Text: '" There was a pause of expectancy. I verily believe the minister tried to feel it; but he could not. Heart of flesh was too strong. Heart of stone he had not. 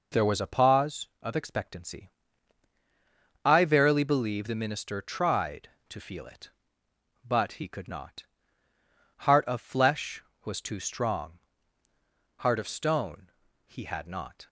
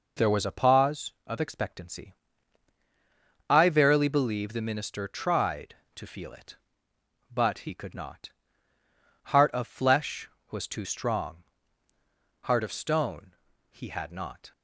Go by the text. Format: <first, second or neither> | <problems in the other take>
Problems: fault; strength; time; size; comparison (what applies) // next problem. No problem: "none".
neither | pauses between "stone" and "he"; the same in both